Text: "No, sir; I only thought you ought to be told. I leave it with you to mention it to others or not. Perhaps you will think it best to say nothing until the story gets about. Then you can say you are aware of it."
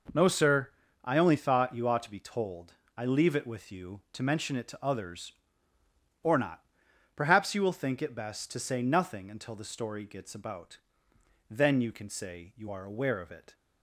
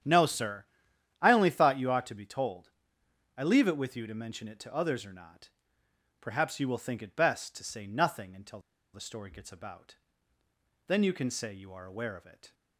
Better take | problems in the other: first | starts louder than the rest; strong; until 1.6 s; 9 dB // pauses between "until" and "the"; slight; at 8.5 s; 0.33 s long

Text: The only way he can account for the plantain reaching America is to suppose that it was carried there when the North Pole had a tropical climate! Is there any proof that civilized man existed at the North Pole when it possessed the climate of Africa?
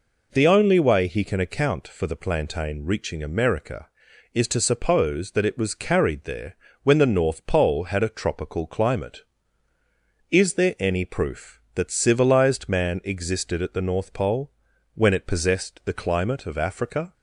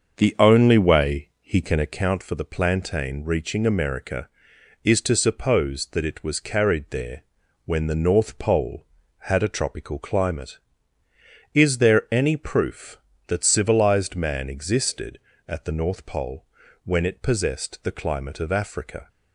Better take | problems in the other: first | starts louder than the rest; until 2.1 s; 6.5 dB // pauses between "there" and "when"; at 7.2 s; 0.42 s long; slight in the first // pauses between "Pole" and "when"; at 16.4 s; 0.40 s long; noticeable in the first

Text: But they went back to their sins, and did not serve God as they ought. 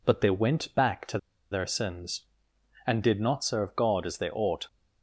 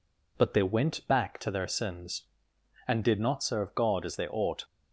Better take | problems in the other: second | pauses between "to" and "their"; slight; at 1.1 s; 0.33 s long

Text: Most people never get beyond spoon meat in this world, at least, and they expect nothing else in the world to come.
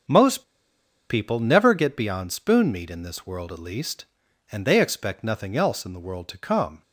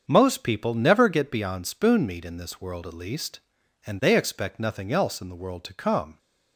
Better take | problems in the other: second | starts louder than the rest; until 1.7 s; 7 dB; also in the second // pauses between "Most" and "people"; noticeable; at 0.4 s; 0.67 s long

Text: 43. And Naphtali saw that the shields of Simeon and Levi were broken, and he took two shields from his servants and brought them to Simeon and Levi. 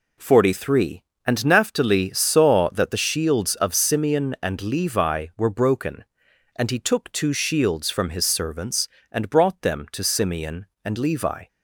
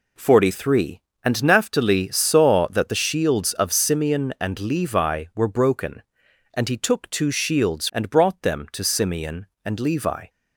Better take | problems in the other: first | skips "from his servants"; at 7.8 s

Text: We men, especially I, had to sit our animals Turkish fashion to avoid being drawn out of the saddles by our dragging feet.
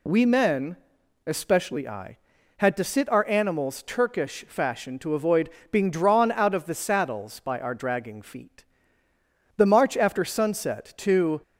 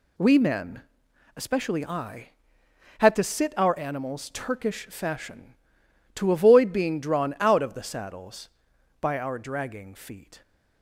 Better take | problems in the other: second | pauses between "avoid" and "being"; slight; at 5.4 s; 0.24 s long // goes on to say "The march after sunset to"; strong; from 9.5 s on; 1.8 s long

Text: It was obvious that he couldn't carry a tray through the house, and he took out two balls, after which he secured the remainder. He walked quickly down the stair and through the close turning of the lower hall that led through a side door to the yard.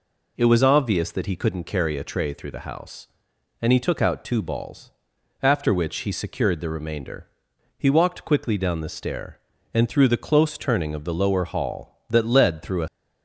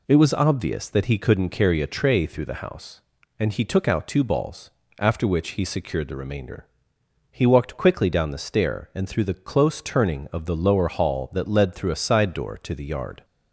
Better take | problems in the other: second | stops before "side door to the yard"; at 12.8 s

